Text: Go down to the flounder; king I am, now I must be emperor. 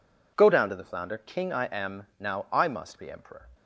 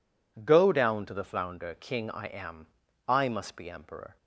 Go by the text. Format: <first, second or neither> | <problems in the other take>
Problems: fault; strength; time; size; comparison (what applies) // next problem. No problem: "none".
first | skips "now"; at 2.8 s